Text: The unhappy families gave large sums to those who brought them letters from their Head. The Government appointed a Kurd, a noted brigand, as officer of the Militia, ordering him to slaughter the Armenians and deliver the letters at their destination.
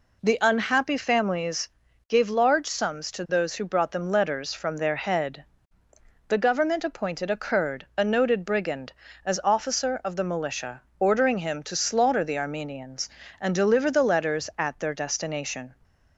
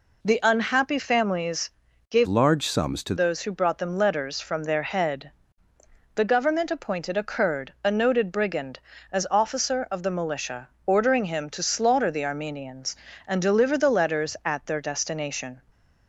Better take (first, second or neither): first